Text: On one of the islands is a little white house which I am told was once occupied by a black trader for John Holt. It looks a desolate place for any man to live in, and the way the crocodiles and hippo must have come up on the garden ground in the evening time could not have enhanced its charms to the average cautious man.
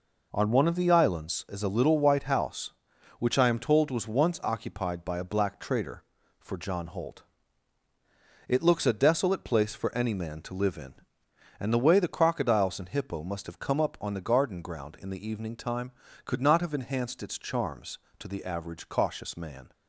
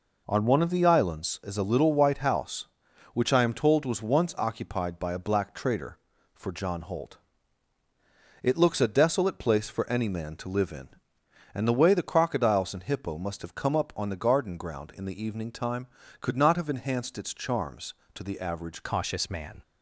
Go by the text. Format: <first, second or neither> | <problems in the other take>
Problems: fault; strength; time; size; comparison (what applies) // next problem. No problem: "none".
first | changes voice at "cautious"; from 18.8 s on; 0.8 s long